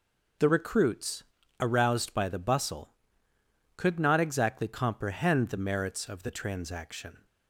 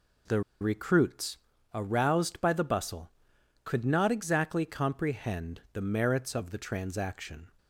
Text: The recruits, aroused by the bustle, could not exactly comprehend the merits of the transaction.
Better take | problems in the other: first | pauses between "The" and "recruits"; slight; at 0.4 s; 0.20 s long

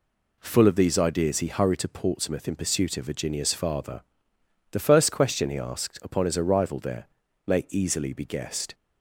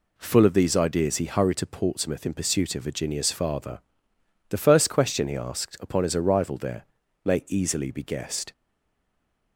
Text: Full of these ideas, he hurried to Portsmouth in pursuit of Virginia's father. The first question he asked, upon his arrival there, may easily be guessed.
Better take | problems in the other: first | stays silent after the last word; from 8.5 s on; 1.0 s long

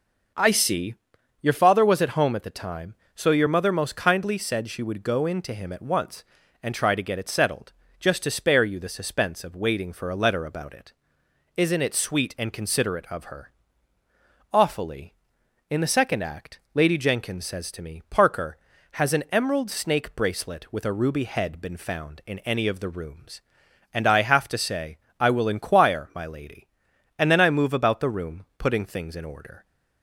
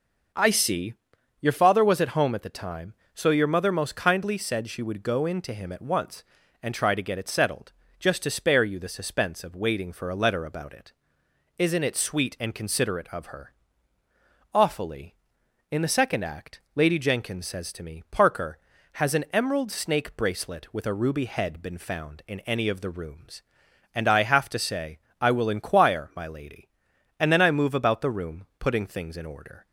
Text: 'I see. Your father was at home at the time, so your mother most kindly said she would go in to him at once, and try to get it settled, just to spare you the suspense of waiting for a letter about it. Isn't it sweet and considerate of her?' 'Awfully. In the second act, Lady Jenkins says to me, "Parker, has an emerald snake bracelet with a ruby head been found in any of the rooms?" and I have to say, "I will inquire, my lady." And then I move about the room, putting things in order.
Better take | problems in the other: neither | none

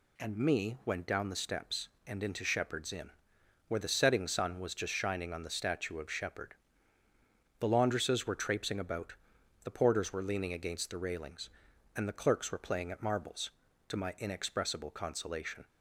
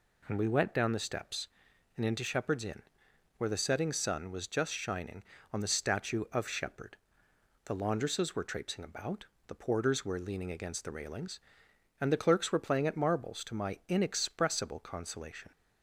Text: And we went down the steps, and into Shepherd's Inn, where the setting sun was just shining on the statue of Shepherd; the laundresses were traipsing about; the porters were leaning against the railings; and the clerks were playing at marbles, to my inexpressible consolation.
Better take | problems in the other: second | says "me" for "we"; at 0.3 s

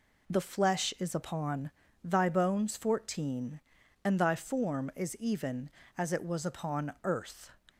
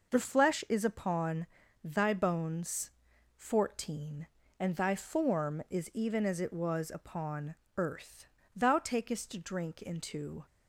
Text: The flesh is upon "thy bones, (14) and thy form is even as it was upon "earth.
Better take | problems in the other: first | pauses between "upon" and "thy"; slight; at 1.4 s; 0.36 s long; slight in the first // pauses between "upon" and "earth"; slight; at 7.5 s; 0.24 s long // goes on to say "Thou takest drink into"; strong; from 8.5 s on; 1.9 s long

